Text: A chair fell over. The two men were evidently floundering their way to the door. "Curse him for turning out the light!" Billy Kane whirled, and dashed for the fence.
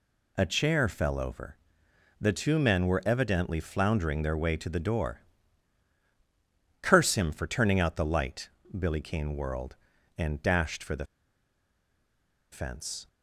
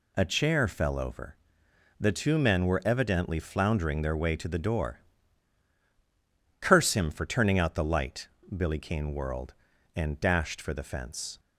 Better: second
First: pauses between "the" and "fence"; strong; at 11.0 s; 1.4 s long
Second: none

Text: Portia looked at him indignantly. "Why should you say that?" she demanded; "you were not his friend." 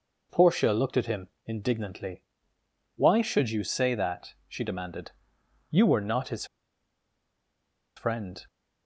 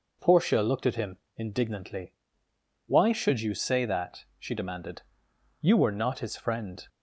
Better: second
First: pauses between "him" and "indignantly"; slight; at 1.2 s; 0.20 s long // pauses between "his" and "friend"; strong; at 6.4 s; 1.5 s long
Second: pauses between "him" and "indignantly"; slight; at 1.1 s; 0.21 s long

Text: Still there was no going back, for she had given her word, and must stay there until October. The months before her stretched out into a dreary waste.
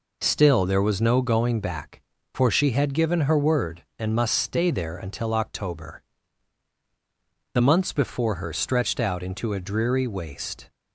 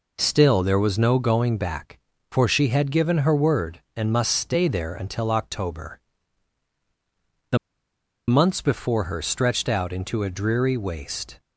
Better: first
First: none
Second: pauses between "The" and "months"; noticeable; at 7.5 s; 0.70 s long

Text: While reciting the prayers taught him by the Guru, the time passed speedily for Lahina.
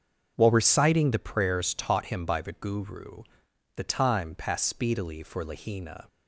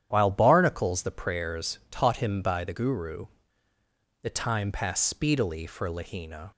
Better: first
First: starts louder than the rest; until 1.3 s; 6.5 dB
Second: starts louder than the rest; strong; until 1.1 s; 10 dB // says "barnacles" for "reciting"; at 0.2 s

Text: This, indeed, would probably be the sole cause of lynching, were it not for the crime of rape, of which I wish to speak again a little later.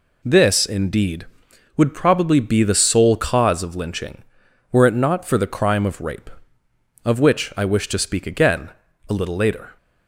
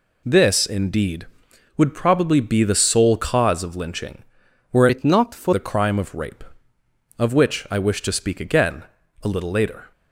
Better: first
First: pauses between "again" and "a"; at 8.6 s; 0.38 s long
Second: changes voice from "it" to "for"; from 4.8 to 5.5 s; 0.7 s long // pauses between "again" and "a"; at 8.8 s; 0.38 s long

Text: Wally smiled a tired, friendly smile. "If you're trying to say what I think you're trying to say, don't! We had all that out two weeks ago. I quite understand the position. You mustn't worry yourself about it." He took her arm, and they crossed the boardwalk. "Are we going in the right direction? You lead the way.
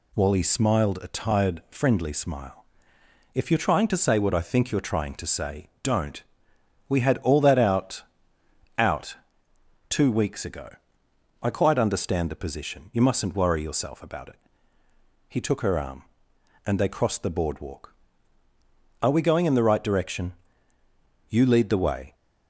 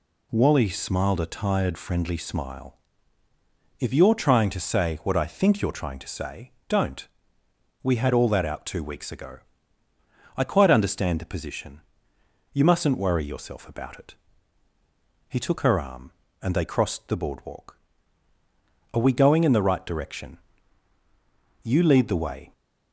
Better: second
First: says "out" twice; at 8.7 s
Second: none

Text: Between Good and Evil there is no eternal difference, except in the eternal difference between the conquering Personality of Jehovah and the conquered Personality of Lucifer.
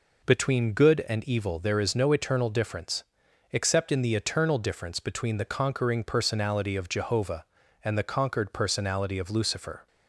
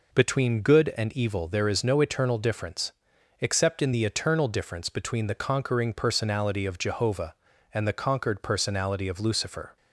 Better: neither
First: none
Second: none

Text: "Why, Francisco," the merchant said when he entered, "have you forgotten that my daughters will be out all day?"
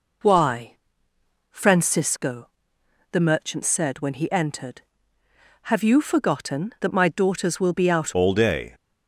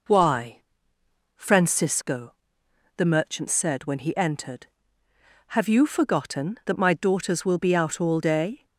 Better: second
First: changes voice at "all"; from 8.1 s on; 0.6 s long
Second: none

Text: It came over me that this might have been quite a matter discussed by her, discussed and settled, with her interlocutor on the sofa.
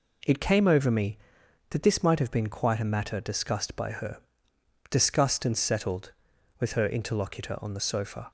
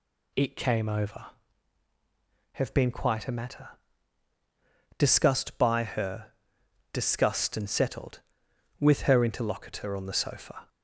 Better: first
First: none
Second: skips "me that this might"; at 1.8 s // pauses between "matter" and "discussed"; strong; at 3.6 s; 1.2 s long

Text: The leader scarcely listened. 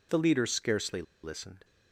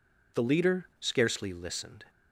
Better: second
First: pauses between "scarcely" and "listened"; slight; at 1.0 s; 0.21 s long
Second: none

